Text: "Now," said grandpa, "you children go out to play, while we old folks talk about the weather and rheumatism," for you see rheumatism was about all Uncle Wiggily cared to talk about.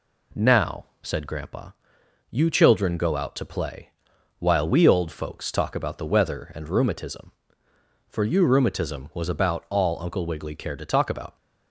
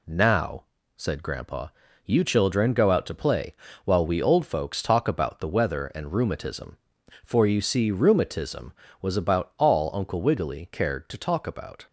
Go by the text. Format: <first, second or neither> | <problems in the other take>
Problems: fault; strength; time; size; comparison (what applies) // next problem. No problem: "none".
second | skips "see"; at 8.4 s